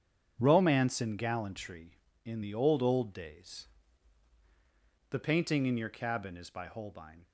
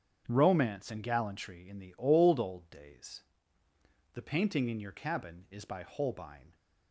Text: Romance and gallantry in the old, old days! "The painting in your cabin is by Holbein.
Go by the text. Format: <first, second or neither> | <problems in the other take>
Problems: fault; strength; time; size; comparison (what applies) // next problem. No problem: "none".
neither | starts louder than the rest; strong; the same in both